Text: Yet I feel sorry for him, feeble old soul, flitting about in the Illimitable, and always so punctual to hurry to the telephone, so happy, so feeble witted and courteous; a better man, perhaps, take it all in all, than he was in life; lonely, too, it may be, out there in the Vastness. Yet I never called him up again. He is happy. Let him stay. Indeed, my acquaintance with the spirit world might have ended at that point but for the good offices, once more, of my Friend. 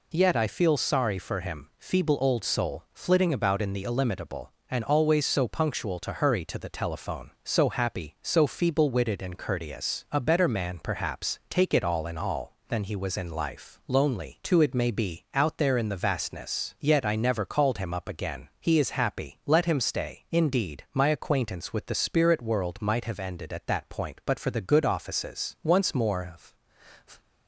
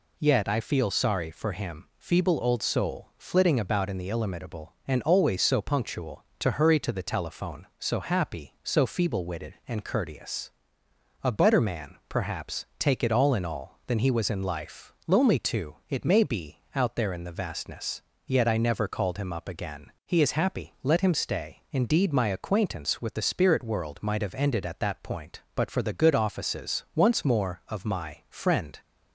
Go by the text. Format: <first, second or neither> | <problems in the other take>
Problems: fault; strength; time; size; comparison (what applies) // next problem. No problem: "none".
second | stops before "my Friend"; at 27.2 s